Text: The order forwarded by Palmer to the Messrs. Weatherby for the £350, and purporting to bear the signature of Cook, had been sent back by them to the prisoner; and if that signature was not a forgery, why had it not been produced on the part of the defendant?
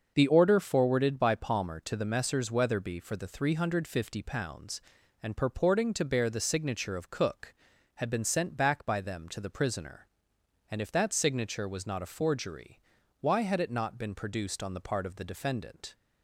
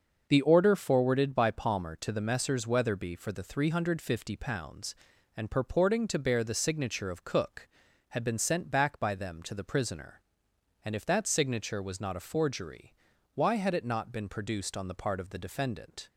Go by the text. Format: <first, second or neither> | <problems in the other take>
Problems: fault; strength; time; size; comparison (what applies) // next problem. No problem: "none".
neither | starts louder than the rest; the same in both